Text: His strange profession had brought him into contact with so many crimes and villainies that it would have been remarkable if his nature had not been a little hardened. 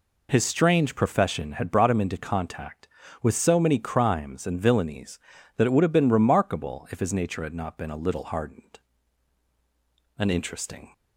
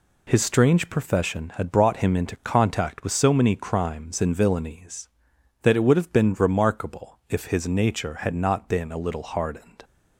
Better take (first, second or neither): second